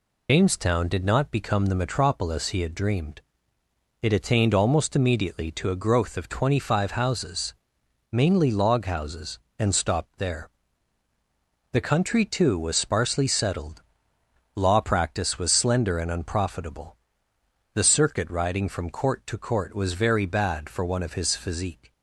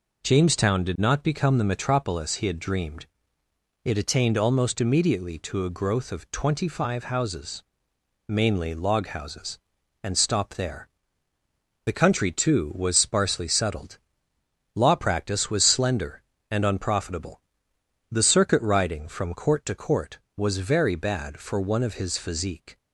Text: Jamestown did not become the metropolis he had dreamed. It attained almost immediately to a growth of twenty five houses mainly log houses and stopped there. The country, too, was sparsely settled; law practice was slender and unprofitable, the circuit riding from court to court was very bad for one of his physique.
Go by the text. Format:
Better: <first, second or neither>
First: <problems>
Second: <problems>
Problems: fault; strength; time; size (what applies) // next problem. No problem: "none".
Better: second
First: loses the start of "Jamestown"; at 0.2 s; 95 ms // pauses between "houses" and "mainly"; noticeable; at 7.5 s; 0.56 s long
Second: pauses between "houses" and "mainly"; noticeable; at 7.6 s; 0.64 s long